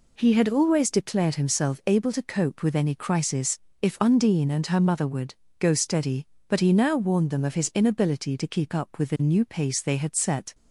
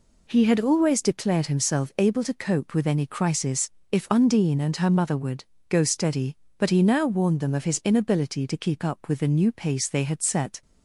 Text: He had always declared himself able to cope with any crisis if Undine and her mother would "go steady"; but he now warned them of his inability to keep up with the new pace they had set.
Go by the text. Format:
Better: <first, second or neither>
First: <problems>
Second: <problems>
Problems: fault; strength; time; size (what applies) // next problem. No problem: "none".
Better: neither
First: pauses between "crisis" and "if"; slight; at 3.5 s; 0.22 s long // pauses between "would" and "go"; slight; at 5.3 s; 0.26 s long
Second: pauses between "crisis" and "if"; slight; at 3.7 s; 0.20 s long // pauses between "would" and "go"; slight; at 5.4 s; 0.26 s long